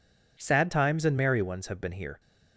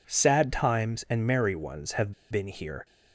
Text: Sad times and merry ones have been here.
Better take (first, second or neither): first